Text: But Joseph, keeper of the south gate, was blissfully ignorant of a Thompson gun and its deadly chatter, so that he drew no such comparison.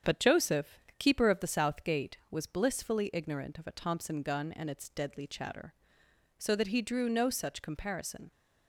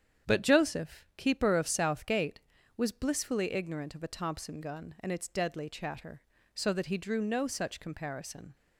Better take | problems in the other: first | starts louder than the rest; strong; until 1.3 s; 8.5 dB; strong in the first // skips "the"; at 1.6 s

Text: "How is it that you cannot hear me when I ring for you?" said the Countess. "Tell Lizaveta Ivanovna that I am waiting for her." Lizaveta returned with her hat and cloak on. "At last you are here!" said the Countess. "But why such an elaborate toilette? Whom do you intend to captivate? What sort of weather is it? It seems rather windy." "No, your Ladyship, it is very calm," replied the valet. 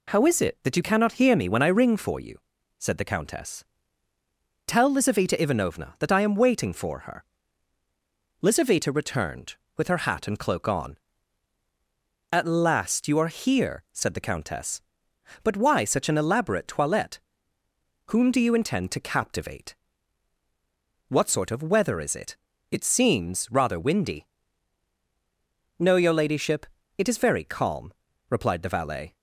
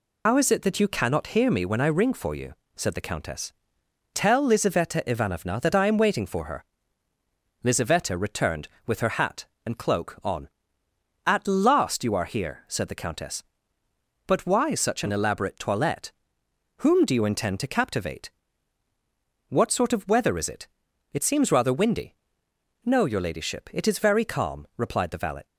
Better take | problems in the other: first | loses the start of "How"; at 0.2 s; 95 ms

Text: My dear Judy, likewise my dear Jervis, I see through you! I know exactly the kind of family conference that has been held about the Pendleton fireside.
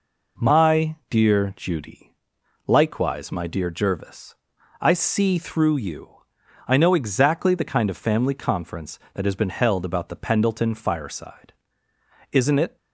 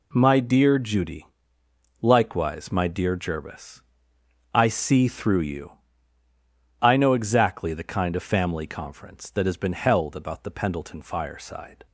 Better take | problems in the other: second | goes on to say "Isn't it"; slight; from 12.3 s on; 0.44 s long

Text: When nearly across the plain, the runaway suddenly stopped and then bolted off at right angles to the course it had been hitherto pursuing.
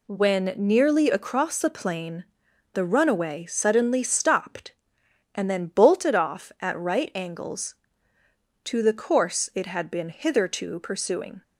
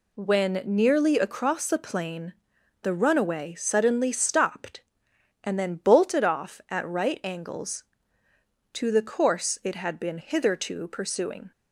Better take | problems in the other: neither | none

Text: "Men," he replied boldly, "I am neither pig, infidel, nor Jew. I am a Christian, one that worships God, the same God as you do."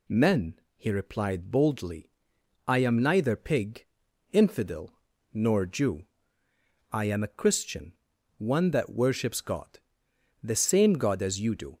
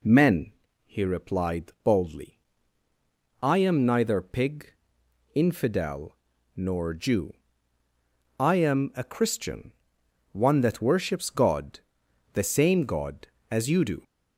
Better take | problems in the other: neither | none

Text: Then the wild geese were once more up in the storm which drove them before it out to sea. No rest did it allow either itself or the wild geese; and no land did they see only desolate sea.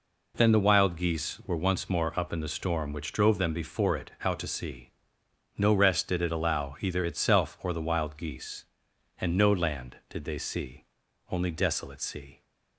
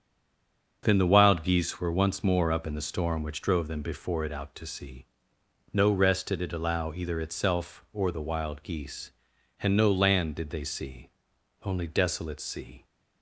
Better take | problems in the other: first | stays silent before the first word; slight; until 0.8 s; 0.8 s long // starts louder than the rest; until 1.8 s; 6.5 dB // pauses between "see" and "only"; noticeable; at 11.0 s; 0.54 s long; noticeable in the first

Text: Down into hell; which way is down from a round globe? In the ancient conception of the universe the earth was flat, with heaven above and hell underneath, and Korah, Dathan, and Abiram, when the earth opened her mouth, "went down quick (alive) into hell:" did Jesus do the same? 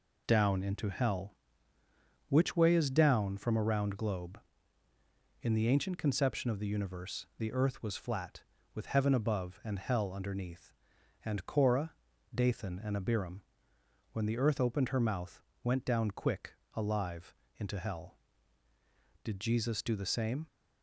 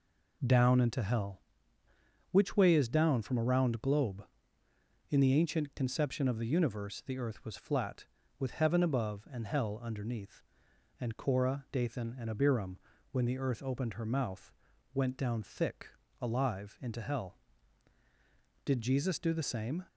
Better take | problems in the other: first | says "thick" for "quick"; at 15.4 s

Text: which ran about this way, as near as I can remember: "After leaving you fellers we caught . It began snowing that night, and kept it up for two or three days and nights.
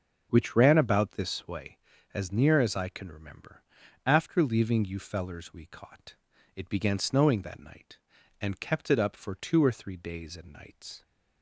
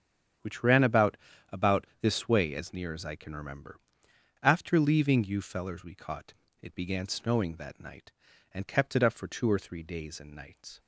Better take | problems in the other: first | starts louder than the rest; strong; until 1.7 s; 8.5 dB; also in the first // says "about" twice; at 1.5 s

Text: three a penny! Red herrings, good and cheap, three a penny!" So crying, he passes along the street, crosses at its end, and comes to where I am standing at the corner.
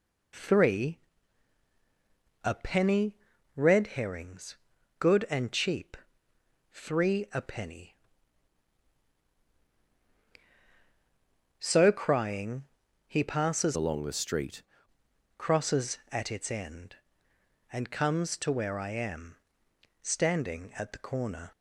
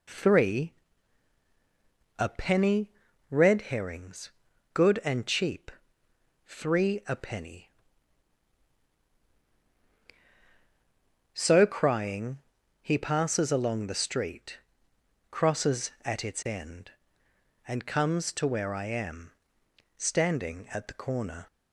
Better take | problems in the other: second | pauses between "three" and "a"; strong; at 0.9 s; 1.4 s long; strong in the second // changes voice from "along" to "street"; from 13.7 to 14.6 s; 0.9 s long // pauses between "am" and "standing"; noticeable; at 19.3 s; 0.66 s long; noticeable in the second

